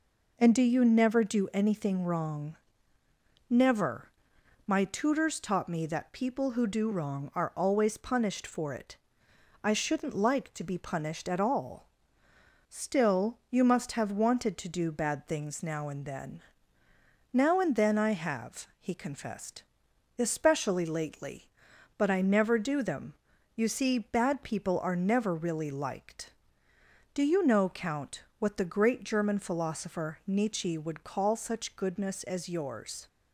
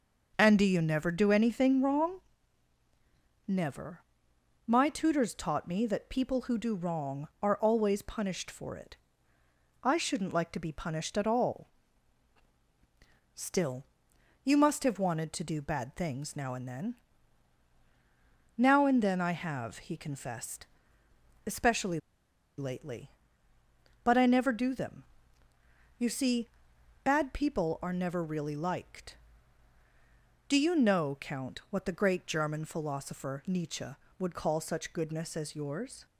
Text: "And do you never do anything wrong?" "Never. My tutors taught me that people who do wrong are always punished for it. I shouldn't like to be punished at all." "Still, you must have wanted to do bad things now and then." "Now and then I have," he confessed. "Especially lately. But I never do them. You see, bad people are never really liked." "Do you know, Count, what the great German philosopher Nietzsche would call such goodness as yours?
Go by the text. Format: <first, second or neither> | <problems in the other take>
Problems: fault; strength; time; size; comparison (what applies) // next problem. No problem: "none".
first | starts louder than the rest; noticeable; until 1.3 s; 6 dB // pauses between "Especially" and "lately"; noticeable; at 21.9 s; 0.58 s long